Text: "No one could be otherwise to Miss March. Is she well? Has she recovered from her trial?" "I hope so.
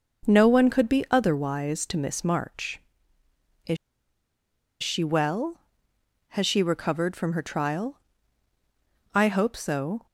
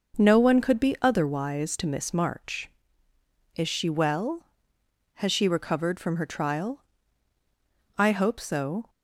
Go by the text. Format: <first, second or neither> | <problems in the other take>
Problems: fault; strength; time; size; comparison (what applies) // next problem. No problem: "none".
second | pauses between "Is" and "she"; at 3.7 s; 1.0 s long